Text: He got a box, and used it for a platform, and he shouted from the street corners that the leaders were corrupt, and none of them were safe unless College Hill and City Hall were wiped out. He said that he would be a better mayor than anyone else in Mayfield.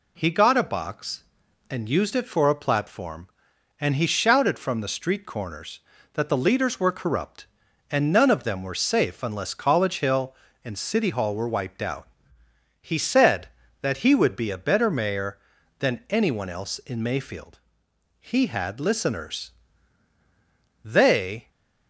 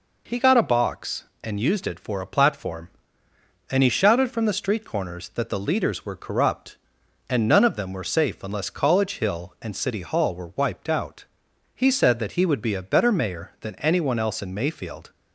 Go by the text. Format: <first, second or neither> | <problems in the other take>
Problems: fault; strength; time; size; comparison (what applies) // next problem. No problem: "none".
second | goes on to say "He had listeners They"; strong; from 18.2 s on; 3.2 s long